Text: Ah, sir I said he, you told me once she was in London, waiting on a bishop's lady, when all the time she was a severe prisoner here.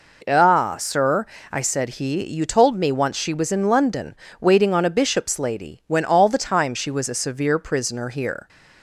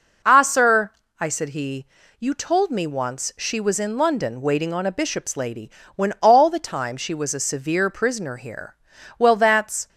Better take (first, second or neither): first